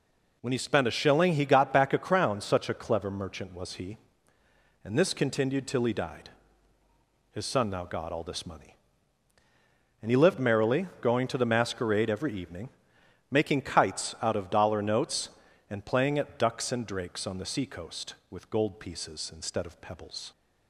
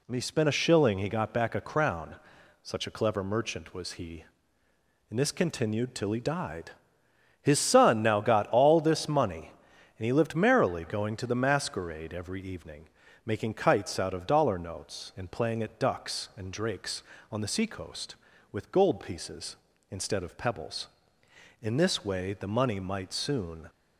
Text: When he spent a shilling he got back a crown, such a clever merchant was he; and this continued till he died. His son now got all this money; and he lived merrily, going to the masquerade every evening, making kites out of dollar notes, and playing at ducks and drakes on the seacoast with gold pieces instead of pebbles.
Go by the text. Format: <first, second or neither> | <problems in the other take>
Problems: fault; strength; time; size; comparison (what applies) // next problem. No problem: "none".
first | goes on to say "In this way the money might soon"; strong; from 21.6 s on; 2.0 s long